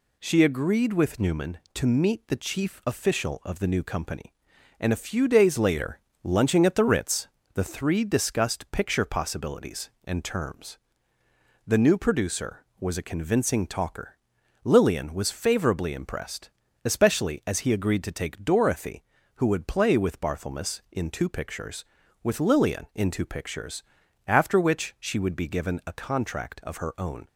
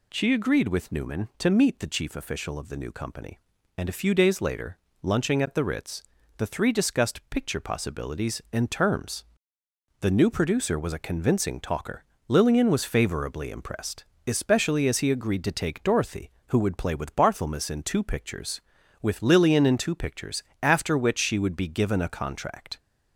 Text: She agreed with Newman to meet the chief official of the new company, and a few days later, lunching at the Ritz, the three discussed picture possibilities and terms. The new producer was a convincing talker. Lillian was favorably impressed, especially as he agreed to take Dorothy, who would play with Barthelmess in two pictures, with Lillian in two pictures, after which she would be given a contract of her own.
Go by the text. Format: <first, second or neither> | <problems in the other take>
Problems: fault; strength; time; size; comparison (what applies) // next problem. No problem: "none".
first | stops before "of her own"; at 22.7 s